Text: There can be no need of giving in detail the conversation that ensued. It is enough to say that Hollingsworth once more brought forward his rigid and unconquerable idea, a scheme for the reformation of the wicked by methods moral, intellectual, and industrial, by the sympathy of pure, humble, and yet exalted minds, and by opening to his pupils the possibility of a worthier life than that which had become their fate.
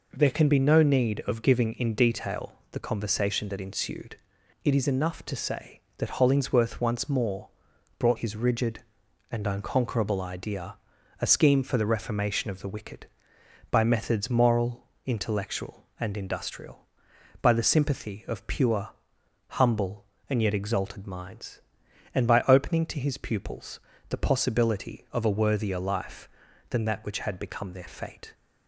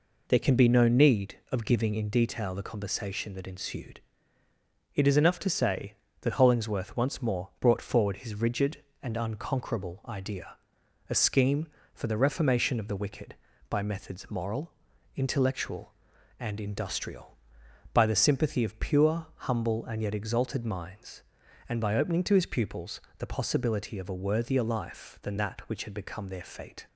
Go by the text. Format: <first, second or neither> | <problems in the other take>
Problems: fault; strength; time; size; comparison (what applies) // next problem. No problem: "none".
second | pauses between "detail" and "the"; slight; at 2.5 s; 0.20 s long // pauses between "more" and "brought"; noticeable; at 7.4 s; 0.50 s long // skips "forward"; at 8.1 s // pauses between "pupils" and "the"; slight; at 23.7 s; 0.30 s long; slight in the second